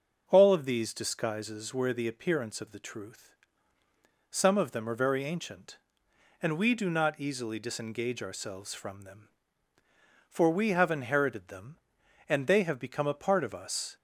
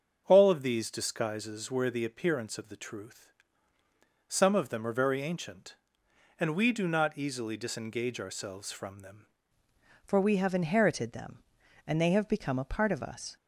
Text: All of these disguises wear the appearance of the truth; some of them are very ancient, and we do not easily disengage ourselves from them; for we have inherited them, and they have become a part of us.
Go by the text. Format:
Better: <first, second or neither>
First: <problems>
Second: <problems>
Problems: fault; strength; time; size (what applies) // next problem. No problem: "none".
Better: first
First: starts louder than the rest; until 1.2 s; 6 dB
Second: starts louder than the rest; until 1.2 s; 7 dB // changes voice at "for"; from 10.0 s on; 3.3 s long